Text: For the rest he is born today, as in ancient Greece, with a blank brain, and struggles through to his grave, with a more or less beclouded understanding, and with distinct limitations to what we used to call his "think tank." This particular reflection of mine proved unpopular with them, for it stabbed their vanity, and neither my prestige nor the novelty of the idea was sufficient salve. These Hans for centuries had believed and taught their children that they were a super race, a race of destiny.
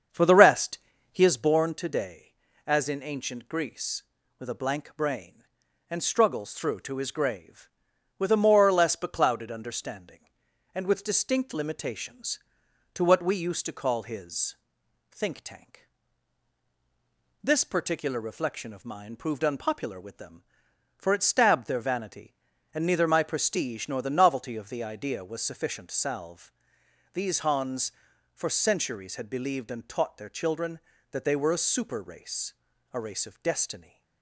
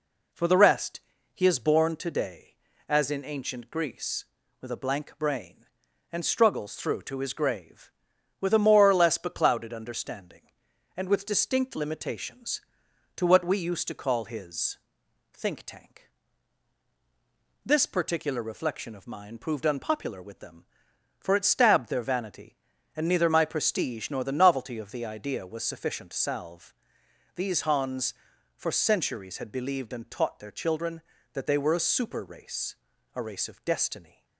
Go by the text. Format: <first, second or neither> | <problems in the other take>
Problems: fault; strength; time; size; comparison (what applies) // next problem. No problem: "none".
second | starts louder than the rest; strong; until 1.4 s; 7 dB // pauses between "rest" and "he"; slight; at 0.7 s; 0.34 s long; slight in the second // pauses between "his" and "think"; noticeable; at 14.5 s; 0.54 s long; noticeable in the second